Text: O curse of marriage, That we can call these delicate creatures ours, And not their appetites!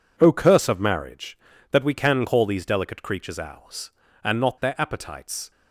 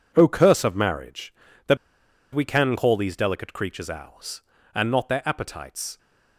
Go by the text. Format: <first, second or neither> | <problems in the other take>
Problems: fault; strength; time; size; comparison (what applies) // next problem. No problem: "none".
first | pauses between "That" and "we"; noticeable; at 1.7 s; 0.56 s long